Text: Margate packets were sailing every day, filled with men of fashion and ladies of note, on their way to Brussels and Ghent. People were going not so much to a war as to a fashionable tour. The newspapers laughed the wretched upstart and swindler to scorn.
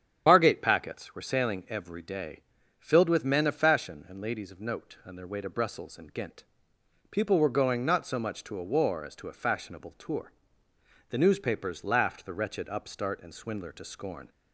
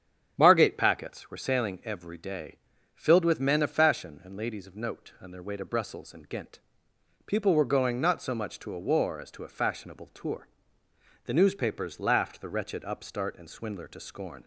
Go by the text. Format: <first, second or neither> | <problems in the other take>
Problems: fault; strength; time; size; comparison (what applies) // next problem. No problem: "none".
second | loses the start of "Margate"; at 0.2 s; 35 ms // starts louder than the rest; strong; until 1.2 s; 8.5 dB; strong in the second